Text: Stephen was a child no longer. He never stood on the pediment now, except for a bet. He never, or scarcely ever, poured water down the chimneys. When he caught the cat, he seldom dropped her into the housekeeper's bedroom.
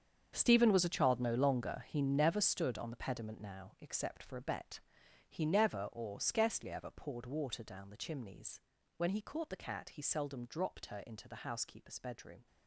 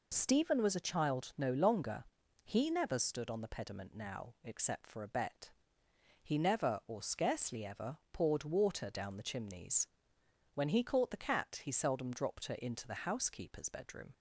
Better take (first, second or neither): second